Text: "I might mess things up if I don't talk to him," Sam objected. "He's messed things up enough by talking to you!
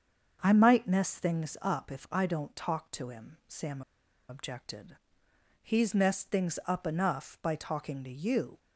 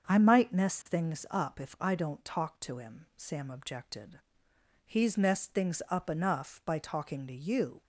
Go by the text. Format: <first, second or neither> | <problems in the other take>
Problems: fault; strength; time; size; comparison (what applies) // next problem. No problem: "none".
second | starts louder than the rest; until 1.4 s; 7 dB; also in the second // pauses between "Sam" and "objected"; noticeable; at 3.8 s; 0.47 s long